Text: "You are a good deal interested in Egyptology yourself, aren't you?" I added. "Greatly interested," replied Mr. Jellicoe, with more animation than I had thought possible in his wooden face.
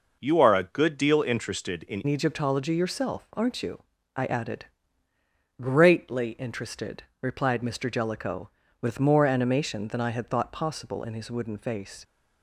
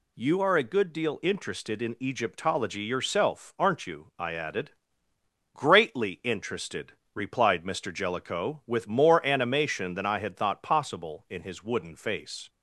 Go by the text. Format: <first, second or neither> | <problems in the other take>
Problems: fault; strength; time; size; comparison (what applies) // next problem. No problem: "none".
second | changes voice at "Egyptology"; from 2.0 s on; 10.0 s long